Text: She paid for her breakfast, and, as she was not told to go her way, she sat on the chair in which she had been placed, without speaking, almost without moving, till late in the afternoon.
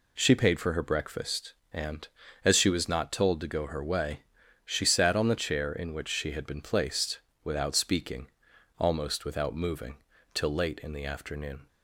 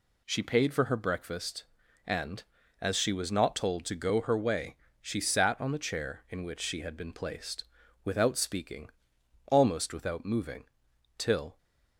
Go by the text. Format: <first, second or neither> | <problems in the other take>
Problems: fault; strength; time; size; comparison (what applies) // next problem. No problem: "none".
first | stops before "late in the afternoon"; at 11.5 s